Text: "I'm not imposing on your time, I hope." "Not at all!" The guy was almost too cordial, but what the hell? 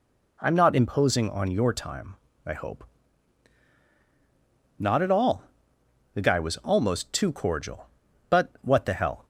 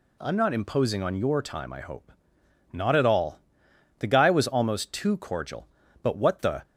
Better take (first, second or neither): first